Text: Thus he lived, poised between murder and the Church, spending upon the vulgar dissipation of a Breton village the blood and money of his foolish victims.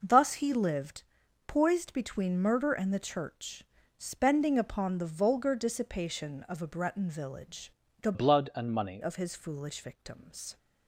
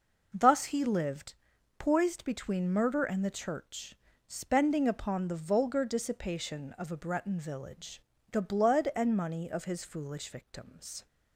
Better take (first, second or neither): second